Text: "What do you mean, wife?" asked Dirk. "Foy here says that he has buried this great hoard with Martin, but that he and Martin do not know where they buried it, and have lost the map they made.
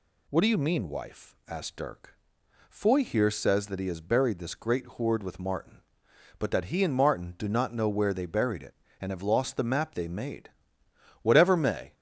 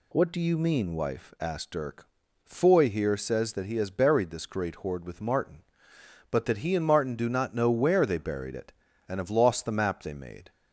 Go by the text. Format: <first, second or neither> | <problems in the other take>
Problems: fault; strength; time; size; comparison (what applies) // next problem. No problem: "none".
second | goes on to say "Whatever may"; noticeable; from 11.2 s on; 0.72 s long